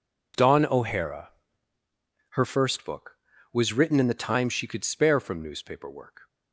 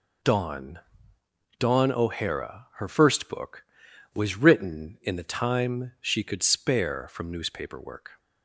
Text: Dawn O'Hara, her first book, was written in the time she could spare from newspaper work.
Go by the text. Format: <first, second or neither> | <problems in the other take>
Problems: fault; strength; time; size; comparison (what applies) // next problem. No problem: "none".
first | says "Dawn" twice; at 1.5 s